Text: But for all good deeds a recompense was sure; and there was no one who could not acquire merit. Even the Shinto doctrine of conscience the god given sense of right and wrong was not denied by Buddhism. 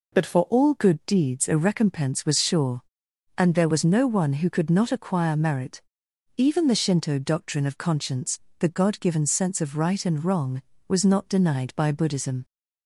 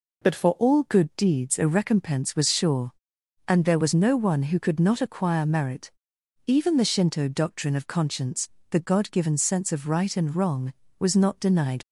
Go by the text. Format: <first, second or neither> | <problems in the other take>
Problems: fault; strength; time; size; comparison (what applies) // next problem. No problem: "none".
first | pauses between "conscience" and "the"; slight; at 8.4 s; 0.22 s long; slight in the first // stops before "by Buddhism"; at 11.8 s